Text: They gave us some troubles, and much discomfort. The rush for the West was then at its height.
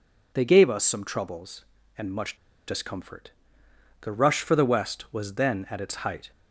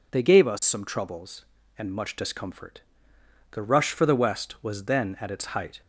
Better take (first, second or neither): second